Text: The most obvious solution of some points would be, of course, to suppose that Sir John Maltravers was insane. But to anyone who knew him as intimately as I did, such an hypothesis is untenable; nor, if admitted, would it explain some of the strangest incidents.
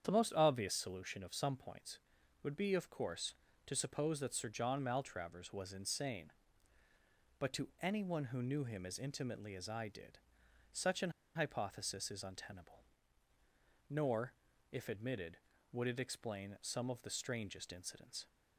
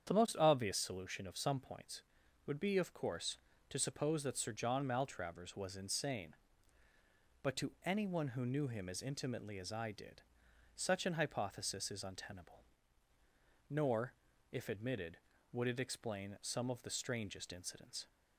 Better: second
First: starts louder than the rest; strong; until 1.0 s; 8.5 dB // pauses between "an" and "hypothesis"; slight; at 11.0 s; 0.25 s long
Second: starts louder than the rest; strong; until 1.1 s; 8.5 dB

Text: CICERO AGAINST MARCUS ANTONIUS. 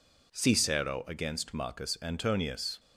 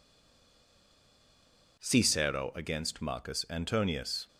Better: first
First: none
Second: stays silent before the first word; noticeable; until 1.7 s; 1.7 s long

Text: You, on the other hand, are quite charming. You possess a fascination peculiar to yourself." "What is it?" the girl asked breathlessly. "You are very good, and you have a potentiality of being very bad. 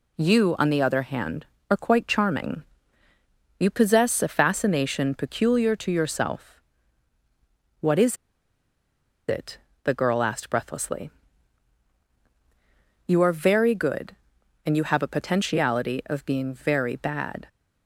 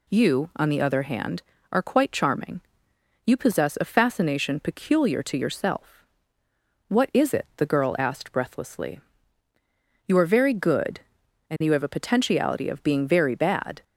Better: second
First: pauses between "is" and "it"; at 8.1 s; 1.1 s long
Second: none

